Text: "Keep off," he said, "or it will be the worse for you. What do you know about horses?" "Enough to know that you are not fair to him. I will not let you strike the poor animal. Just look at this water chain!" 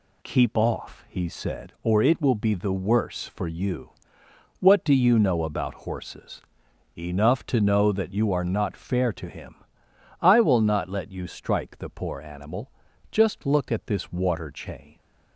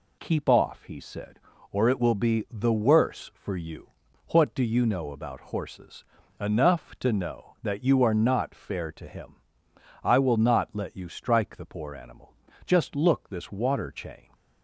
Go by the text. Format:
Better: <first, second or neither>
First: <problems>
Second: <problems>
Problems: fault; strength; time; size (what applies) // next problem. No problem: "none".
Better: first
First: none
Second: skips "at"; at 13.2 s